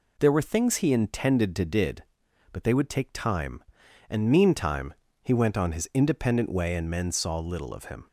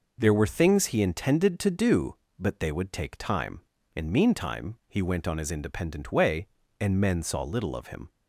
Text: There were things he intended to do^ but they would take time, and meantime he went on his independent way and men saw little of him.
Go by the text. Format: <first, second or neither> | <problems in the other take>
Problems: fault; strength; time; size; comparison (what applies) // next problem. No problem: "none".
second | says "did" for "do"; at 1.6 s // pauses between "meantime" and "he"; slight; at 4.9 s; 0.28 s long